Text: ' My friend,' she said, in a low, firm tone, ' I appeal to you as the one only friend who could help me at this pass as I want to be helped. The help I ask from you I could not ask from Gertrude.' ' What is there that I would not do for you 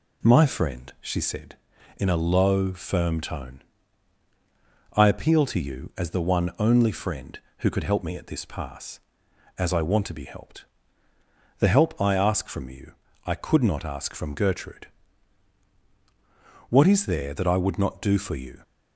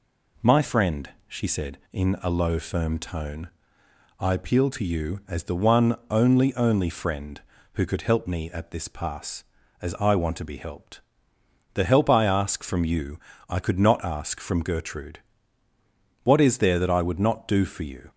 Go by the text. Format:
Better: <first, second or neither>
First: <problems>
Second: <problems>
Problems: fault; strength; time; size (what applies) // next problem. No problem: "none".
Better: first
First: pauses between "you" and "I"; slight; at 12.9 s; 0.34 s long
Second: says "only" twice; at 6.5 s // pauses between "you" and "I"; slight; at 13.1 s; 0.30 s long